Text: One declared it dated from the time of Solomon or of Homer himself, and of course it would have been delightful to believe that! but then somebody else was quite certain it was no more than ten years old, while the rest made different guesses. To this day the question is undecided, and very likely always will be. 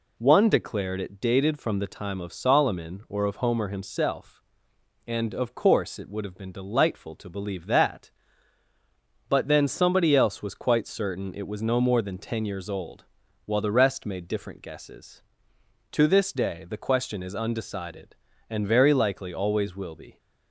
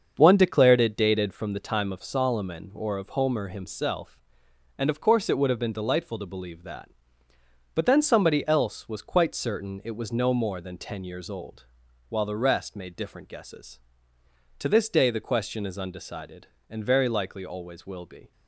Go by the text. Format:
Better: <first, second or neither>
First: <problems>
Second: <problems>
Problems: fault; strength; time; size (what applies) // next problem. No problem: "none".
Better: first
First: none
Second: starts louder than the rest; until 1.4 s; 6.5 dB